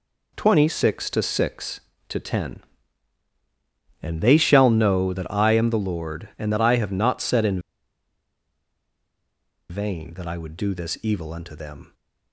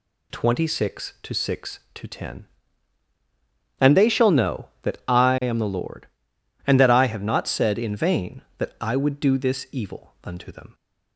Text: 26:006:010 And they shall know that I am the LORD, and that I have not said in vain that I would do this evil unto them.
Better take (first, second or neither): second